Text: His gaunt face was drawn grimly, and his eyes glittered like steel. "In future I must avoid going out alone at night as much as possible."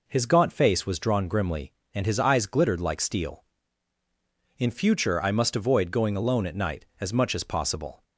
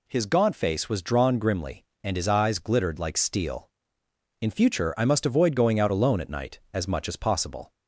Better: second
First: skips "out"; at 6.1 s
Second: none

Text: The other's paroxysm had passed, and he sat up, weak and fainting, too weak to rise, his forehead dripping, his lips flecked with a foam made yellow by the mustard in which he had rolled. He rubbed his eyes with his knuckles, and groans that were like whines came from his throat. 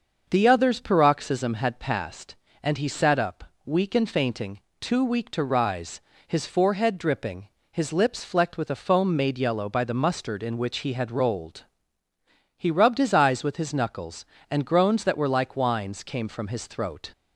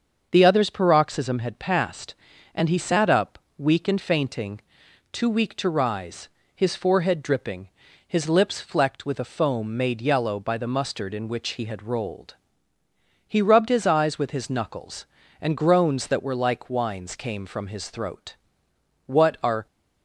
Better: first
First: starts louder than the rest; until 1.2 s; 6 dB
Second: starts louder than the rest; until 1.3 s; 7 dB // goes on to say "What are"; from 19.0 s on; 0.60 s long

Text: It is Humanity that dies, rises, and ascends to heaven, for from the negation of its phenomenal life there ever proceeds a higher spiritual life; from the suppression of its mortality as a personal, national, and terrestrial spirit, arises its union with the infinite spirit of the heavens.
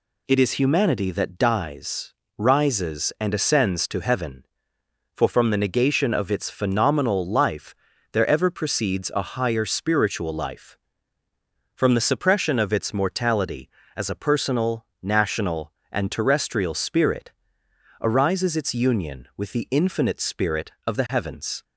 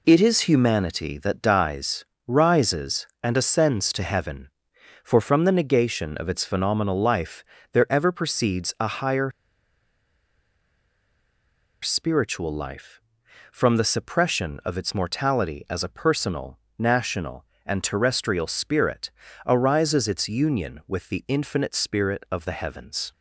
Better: first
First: pauses between "life" and "there"; slight; at 7.7 s; 0.36 s long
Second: pauses between "life" and "there"; slight; at 7.4 s; 0.30 s long // pauses between "higher" and "spiritual"; strong; at 9.3 s; 2.5 s long

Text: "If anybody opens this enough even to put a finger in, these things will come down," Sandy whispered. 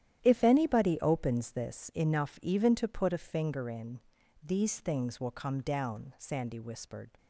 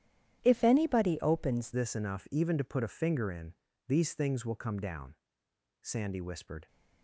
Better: first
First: starts louder than the rest; strong; until 1.2 s; 11 dB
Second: starts louder than the rest; strong; until 1.4 s; 10.5 dB // changes voice at "this"; from 1.7 s on; 4.9 s long

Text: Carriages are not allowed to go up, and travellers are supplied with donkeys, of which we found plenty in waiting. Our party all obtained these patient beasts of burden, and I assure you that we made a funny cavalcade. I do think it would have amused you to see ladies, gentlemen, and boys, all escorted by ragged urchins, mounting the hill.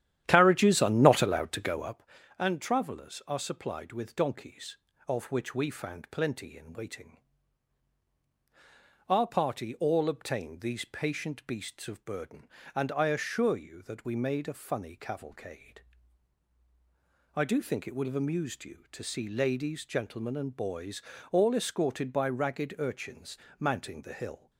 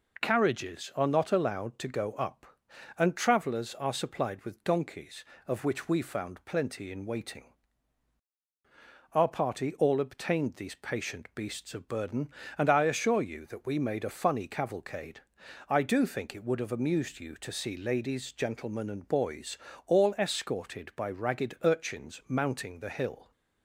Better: second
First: starts louder than the rest; strong; until 2.0 s; 11.5 dB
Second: none

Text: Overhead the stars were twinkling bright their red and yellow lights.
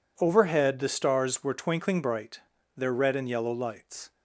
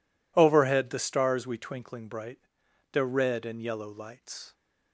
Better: first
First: pauses between "bright" and "their"; slight; at 2.3 s; 0.34 s long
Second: says "we" for "were"; at 1.4 s // pauses between "bright" and "their"; noticeable; at 2.3 s; 0.54 s long

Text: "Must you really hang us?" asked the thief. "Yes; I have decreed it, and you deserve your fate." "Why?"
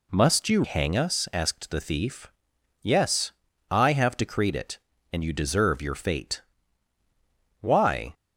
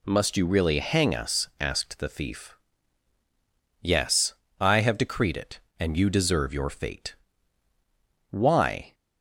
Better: second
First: skips "really"; at 0.6 s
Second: none

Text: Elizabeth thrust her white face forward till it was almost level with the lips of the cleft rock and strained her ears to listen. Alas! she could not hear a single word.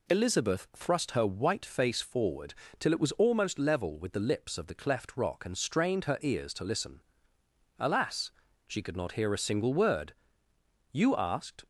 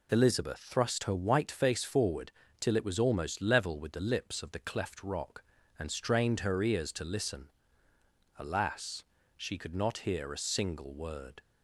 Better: second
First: pauses between "forward" and "till"; slight; at 2.5 s; 0.26 s long // goes on to say "You asked"; noticeable; from 10.9 s on; 0.72 s long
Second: pauses between "forward" and "till"; slight; at 2.3 s; 0.26 s long

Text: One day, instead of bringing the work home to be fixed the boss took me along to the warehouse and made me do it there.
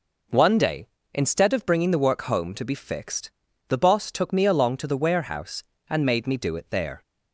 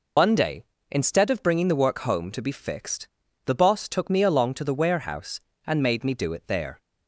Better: first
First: pauses between "fixed" and "the"; at 3.3 s; 0.40 s long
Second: loses the start of "One"; at 0.1 s; 95 ms // pauses between "fixed" and "the"; at 3.0 s; 0.40 s long

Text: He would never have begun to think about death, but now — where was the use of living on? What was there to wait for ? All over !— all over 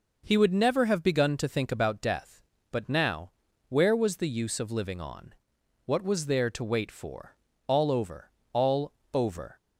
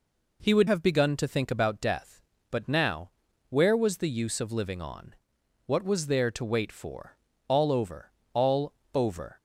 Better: first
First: pauses between "all" and "over"; slight; at 8.9 s; 0.20 s long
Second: skips "never"; at 0.6 s // pauses between "all" and "over"; slight; at 8.7 s; 0.20 s long

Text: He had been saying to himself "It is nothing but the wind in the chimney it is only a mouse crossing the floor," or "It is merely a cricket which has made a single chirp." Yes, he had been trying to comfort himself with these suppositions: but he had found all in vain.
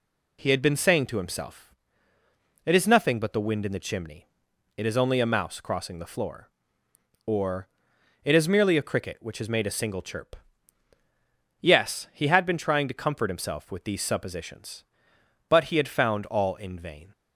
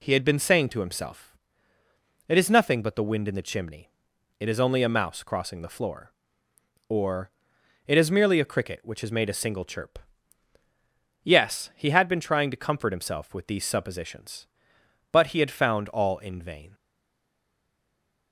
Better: first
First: pauses between "himself" and "It"; noticeable; at 1.7 s; 0.90 s long // pauses between "chimney" and "it"; noticeable; at 4.2 s; 0.52 s long // pauses between "or" and "It"; noticeable; at 7.6 s; 0.56 s long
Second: pauses between "himself" and "It"; noticeable; at 1.3 s; 0.90 s long // pauses between "chimney" and "it"; noticeable; at 3.8 s; 0.52 s long // pauses between "or" and "It"; noticeable; at 7.3 s; 0.56 s long // stays silent after the last word; noticeable; from 16.7 s on; 1.6 s long

